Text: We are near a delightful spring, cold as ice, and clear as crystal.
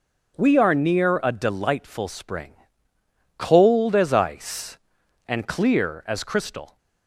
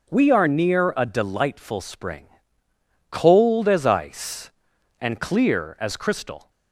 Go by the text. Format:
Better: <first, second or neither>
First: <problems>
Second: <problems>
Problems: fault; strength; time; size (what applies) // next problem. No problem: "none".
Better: neither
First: starts louder than the rest; strong; until 1.3 s; 7.5 dB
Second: starts louder than the rest; strong; until 1.1 s; 7.5 dB